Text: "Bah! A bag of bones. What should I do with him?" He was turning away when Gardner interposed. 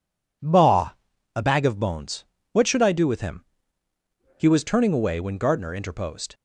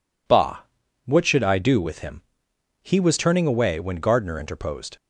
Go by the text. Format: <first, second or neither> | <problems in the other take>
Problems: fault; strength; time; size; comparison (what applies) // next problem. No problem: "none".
first | skips "A bag of bones"; at 0.8 s